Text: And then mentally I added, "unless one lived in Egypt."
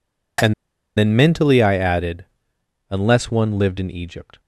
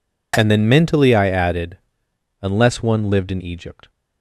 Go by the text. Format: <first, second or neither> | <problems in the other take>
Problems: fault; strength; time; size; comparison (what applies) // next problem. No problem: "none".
second | pauses between "And" and "then"; at 0.5 s; 0.44 s long